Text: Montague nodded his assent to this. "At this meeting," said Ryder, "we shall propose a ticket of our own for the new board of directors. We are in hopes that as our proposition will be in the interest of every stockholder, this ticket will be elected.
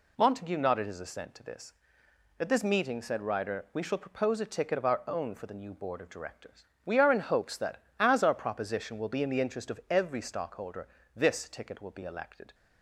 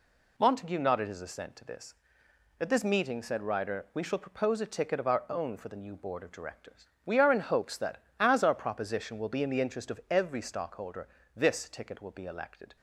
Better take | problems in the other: neither | none

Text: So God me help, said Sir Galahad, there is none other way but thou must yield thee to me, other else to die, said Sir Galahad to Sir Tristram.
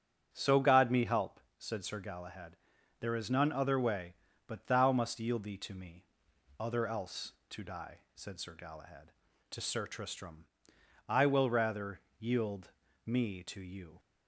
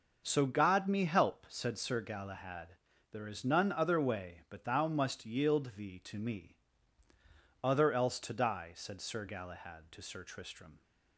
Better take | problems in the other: second | starts louder than the rest; strong; until 1.3 s; 8 dB; also in the second // goes on to say "I will rather yield me to you"; strong; from 11.0 s on; 2.9 s long

